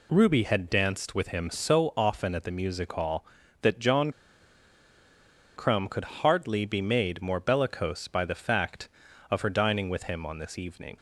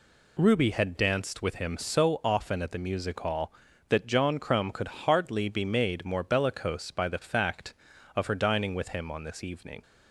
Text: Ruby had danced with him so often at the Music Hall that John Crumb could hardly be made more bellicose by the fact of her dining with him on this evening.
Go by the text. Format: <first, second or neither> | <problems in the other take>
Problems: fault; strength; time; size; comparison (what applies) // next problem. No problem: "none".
second | pauses between "John" and "Crumb"; strong; at 4.1 s; 1.4 s long